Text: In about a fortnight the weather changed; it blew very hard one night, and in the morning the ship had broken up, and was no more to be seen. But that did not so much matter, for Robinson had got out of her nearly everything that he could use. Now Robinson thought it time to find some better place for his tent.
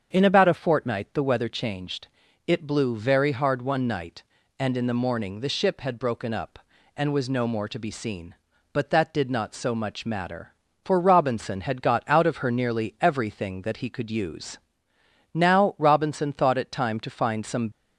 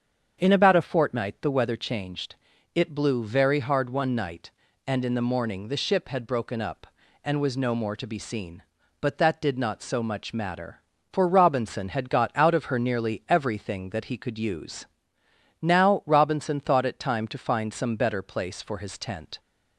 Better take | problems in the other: second | starts louder than the rest; strong; until 1.1 s; 7.5 dB; strong in the second // stops before "better place for his tent"; at 17.7 s

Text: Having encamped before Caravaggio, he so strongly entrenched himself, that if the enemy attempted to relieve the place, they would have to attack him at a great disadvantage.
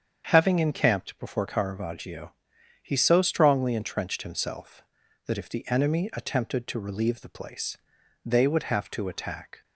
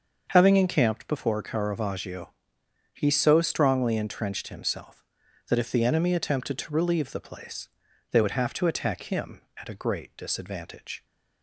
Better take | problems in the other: second | starts louder than the rest; strong; until 1.3 s; 7.5 dB; also in the second // stops before "him at a great disadvantage"; at 9.6 s

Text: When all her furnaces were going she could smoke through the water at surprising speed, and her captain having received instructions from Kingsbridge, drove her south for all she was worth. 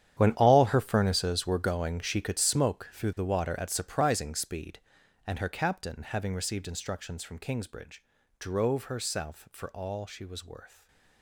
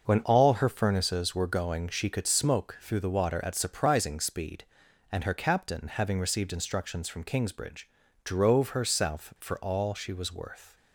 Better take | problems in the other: second | gets quieter; strong; throughout; 16 dB // starts louder than the rest; strong; until 1.1 s; 10 dB; noticeable in the second // stays silent after the last word; slight; from 10.6 s on; 0.6 s long

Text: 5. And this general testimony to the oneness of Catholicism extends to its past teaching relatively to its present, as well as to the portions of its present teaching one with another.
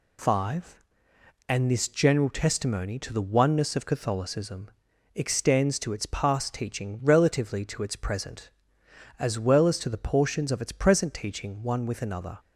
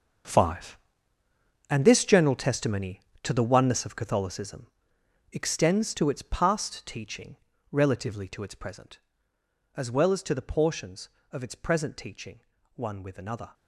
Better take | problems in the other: first | gets quieter; strong; throughout; 13.5 dB // pauses between "Catholicism" and "extends"; noticeable; at 4.6 s; 0.66 s long; noticeable in the first // pauses between "teaching" and "relatively"; slight; at 7.3 s; 0.34 s long // pauses between "teaching" and "one"; slight; at 12.3 s; 0.36 s long

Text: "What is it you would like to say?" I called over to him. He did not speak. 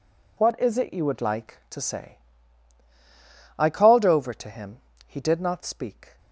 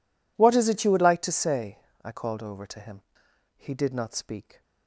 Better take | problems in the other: neither | none

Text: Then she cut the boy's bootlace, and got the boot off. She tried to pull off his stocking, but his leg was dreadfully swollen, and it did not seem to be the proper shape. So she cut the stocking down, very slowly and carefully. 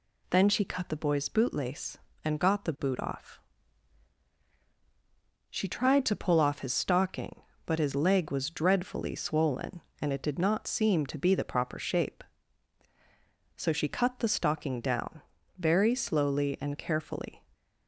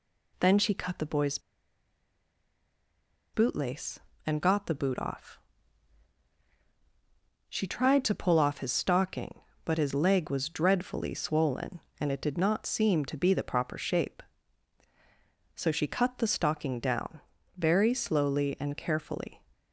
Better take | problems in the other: first | pauses between "boy's" and "bootlace"; strong; at 1.3 s; 1.9 s long

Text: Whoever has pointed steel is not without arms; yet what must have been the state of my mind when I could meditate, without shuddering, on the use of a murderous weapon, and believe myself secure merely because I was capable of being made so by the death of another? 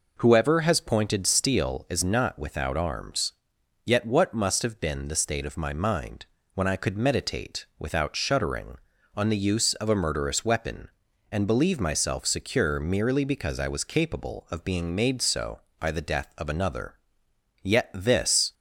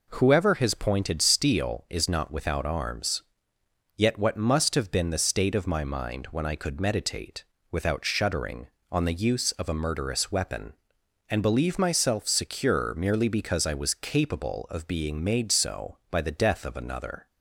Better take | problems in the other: second | pauses between "mind" and "when"; slight; at 6.2 s; 0.30 s long // goes on to say "Yet this"; noticeable; from 17.6 s on; 0.92 s long

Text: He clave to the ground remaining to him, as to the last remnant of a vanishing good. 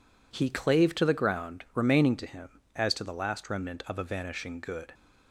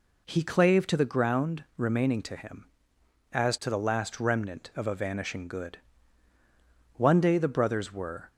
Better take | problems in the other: first | goes on to say "One day the brothers were"; from 6.9 s on; 1.3 s long

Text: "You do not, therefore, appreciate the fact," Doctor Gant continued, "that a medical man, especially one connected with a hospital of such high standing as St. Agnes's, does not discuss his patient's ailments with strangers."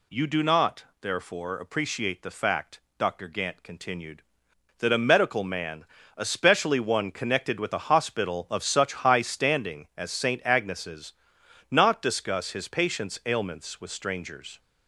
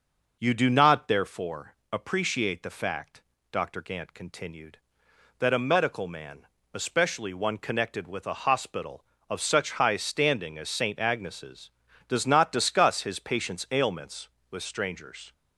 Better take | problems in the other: second | skips "does"; at 11.4 s

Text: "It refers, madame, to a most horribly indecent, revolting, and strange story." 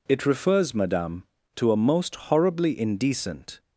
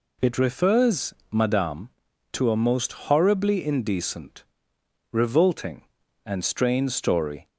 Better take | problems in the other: second | stops before "revolting and strange story"; at 3.5 s

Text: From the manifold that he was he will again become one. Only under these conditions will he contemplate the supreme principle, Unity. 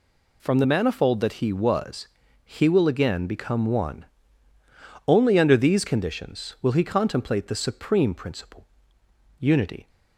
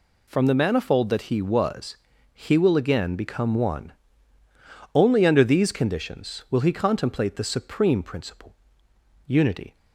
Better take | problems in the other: neither | pauses between "was" and "he"; the same in both

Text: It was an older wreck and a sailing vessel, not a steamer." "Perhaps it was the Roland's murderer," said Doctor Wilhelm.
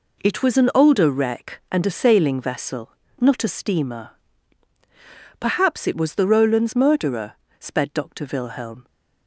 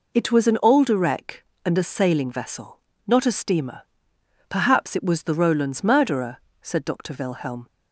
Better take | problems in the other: second | says "sped" for "said"; at 7.5 s

